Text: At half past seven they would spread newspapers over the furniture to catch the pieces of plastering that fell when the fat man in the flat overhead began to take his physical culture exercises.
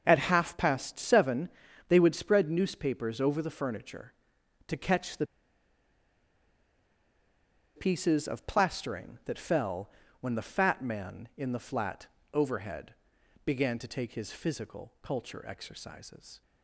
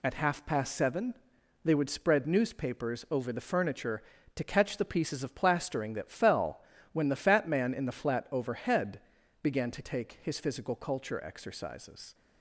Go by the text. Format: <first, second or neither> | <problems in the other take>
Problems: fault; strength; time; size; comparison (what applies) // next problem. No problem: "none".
second | starts louder than the rest; until 1.0 s; 6.5 dB // pauses between "seven" and "they"; at 1.4 s; 0.40 s long; noticeable in the second // pauses between "the" and "pieces"; strong; at 5.2 s; 2.5 s long // pauses between "fell" and "when"; slight; at 9.8 s; 0.32 s long; slight in the second // pauses between "flat" and "overhead"; slight; at 12.0 s; 0.26 s long // pauses between "overhead" and "began"; noticeable; at 12.9 s; 0.50 s long; also in the second